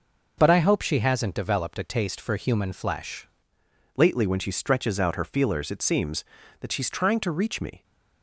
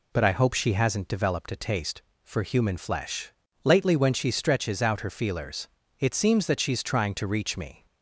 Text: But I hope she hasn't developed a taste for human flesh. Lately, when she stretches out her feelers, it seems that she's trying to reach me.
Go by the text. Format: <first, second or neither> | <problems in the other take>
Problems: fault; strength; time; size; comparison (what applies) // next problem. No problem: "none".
second | changes voice at "Lately"; from 3.9 s on; 3.9 s long